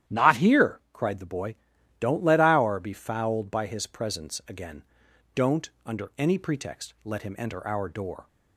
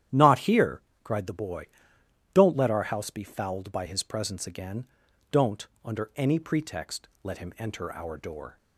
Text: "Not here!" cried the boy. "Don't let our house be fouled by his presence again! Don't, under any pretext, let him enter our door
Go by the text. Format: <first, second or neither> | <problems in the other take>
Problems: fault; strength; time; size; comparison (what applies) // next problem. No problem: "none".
second | starts louder than the rest; strong; until 1.2 s; 11 dB; strong in the second // skips "house"; at 2.7 s